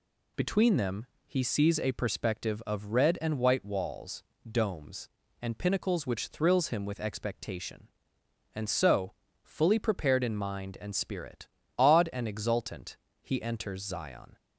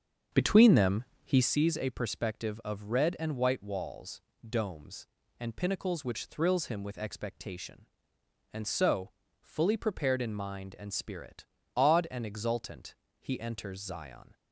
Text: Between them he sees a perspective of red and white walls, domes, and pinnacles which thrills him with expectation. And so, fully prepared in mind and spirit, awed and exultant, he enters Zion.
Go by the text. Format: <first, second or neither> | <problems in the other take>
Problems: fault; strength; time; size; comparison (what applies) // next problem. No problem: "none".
first | starts louder than the rest; until 1.6 s; 7 dB // pauses between "them" and "he"; slight; at 1.0 s; 0.20 s long; slight in the first